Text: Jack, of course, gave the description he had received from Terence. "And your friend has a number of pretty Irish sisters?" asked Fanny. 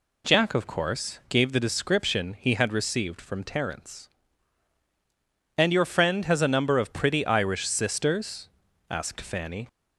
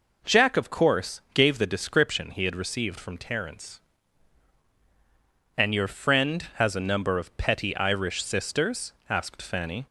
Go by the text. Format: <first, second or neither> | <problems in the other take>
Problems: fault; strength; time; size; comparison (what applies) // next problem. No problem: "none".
first | says "petty" for "pretty"; at 7.3 s